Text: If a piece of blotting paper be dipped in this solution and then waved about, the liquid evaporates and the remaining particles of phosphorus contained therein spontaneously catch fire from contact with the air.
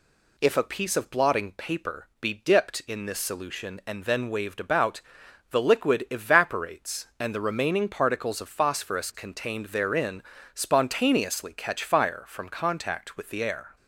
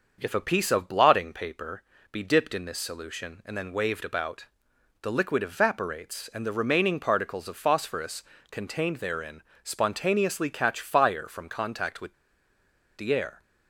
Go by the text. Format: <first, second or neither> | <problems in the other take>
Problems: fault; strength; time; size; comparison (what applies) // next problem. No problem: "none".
first | starts louder than the rest; until 1.2 s; 6.5 dB // pauses between "paper" and "be"; slight; at 1.8 s; 0.30 s long // pauses between "phosphorus" and "contained"; slight; at 8.2 s; 0.30 s long // pauses between "therein" and "spontaneously"; slight; at 9.4 s; 0.22 s long; slight in the first // pauses between "with" and "the"; noticeable; at 12.1 s; 0.83 s long